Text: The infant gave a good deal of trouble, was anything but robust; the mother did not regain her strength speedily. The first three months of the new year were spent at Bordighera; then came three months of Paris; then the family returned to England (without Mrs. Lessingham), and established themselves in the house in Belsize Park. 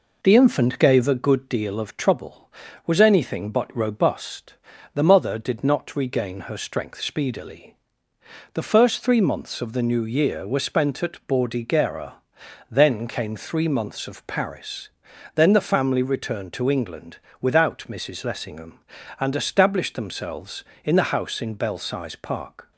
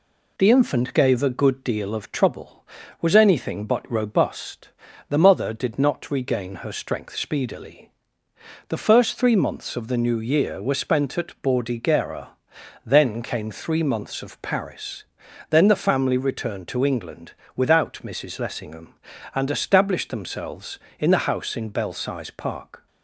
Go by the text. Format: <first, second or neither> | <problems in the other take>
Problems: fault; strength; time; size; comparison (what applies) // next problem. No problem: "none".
second | starts louder than the rest; noticeable; until 1.2 s; 4 dB